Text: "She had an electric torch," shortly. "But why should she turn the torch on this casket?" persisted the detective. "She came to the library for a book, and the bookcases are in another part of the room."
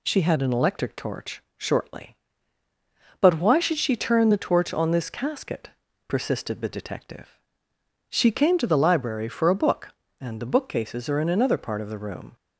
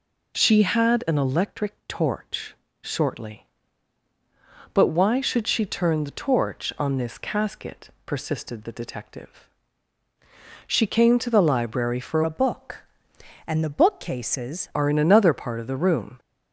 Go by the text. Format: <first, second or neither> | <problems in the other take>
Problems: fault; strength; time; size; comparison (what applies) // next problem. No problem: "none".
first | changes voice from "a" to "bookcases"; from 12.2 to 14.6 s; 2.4 s long